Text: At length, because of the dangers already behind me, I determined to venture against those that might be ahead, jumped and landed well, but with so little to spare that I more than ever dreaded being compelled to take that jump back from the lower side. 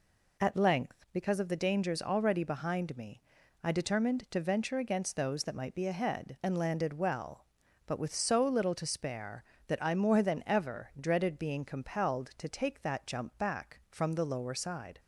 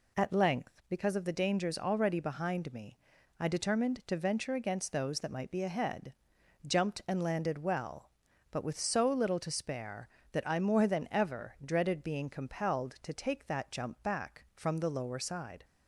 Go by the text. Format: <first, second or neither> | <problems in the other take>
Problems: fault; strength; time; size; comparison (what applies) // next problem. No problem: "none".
second | skips "jumped"; at 6.4 s